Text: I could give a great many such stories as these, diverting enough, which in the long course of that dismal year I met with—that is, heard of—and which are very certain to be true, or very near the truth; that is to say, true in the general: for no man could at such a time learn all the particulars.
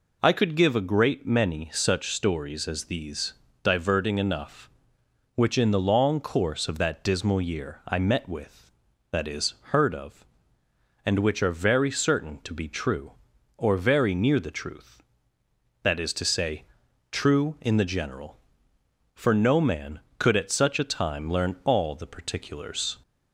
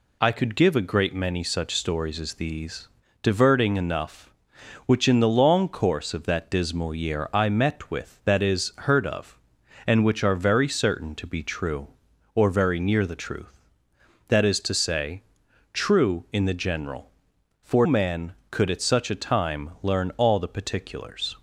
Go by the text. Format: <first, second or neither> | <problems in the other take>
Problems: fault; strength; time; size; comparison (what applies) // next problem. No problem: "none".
first | skips "no"; at 17.8 s